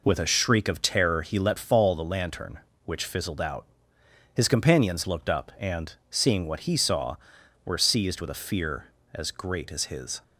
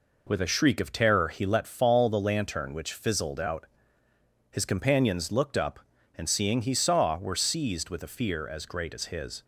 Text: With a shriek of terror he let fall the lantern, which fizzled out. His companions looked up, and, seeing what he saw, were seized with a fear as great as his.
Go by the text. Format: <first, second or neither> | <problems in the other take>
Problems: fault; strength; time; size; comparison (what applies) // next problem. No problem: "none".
first | skips "what"; at 6.6 s